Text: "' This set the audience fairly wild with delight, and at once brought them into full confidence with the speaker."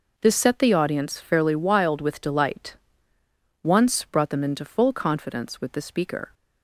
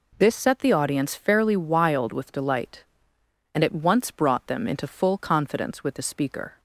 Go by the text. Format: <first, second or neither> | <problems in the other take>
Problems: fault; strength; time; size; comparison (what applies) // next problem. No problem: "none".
second | skips "and at"; at 3.1 s